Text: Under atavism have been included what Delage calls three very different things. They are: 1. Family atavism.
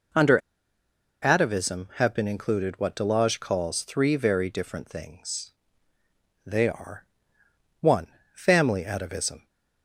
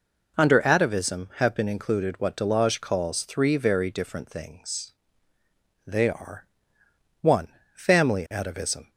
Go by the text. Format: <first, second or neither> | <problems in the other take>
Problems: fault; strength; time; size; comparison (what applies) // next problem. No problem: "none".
second | pauses between "Under" and "atavism"; noticeable; at 0.3 s; 0.84 s long